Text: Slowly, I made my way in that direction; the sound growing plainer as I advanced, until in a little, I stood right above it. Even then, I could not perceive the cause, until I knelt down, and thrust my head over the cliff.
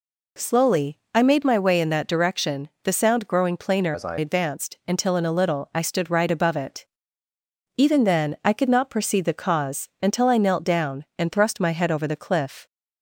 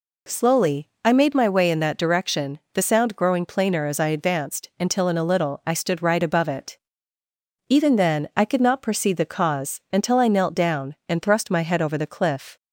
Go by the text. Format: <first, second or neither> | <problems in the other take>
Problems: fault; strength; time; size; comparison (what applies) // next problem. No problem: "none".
second | changes voice from "as" to "I"; from 3.9 to 4.1 s; 0.2 s long